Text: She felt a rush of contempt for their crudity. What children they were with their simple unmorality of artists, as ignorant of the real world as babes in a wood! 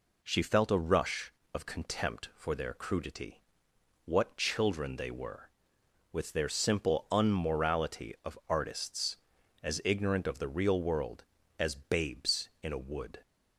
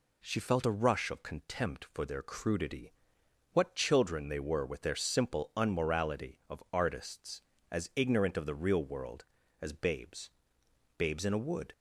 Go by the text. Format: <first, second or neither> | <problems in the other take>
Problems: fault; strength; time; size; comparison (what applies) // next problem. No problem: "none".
first | says "babes" twice; at 10.9 s